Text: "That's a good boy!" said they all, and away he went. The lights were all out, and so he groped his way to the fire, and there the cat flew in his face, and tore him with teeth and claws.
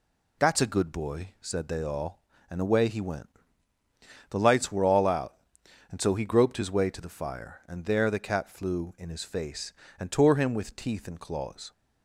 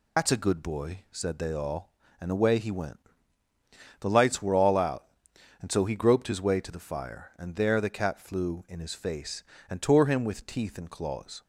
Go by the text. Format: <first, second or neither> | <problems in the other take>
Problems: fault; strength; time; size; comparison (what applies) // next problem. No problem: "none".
first | loses the start of "That's"; at 0.1 s; 65 ms